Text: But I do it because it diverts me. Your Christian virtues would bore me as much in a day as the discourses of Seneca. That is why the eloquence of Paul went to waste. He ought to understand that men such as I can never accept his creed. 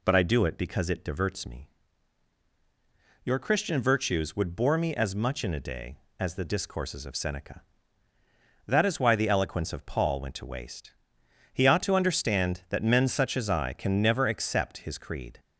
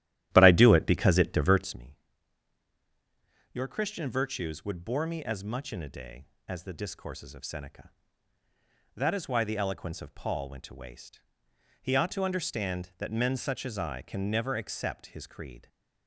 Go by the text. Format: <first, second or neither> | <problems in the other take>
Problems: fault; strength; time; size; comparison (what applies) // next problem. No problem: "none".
first | starts louder than the rest; strong; until 1.8 s; 13 dB